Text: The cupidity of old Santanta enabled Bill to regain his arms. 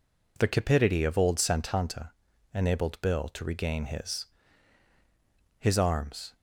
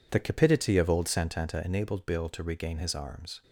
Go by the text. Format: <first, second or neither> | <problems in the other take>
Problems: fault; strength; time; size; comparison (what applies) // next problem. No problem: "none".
second | pauses between "Santanta" and "enabled"; at 2.1 s; 0.42 s long // says "his" twice; at 5.5 s